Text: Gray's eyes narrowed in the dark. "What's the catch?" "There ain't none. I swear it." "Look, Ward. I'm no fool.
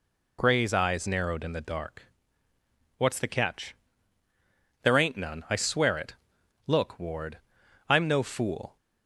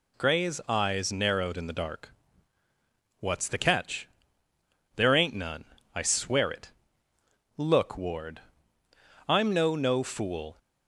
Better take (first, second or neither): first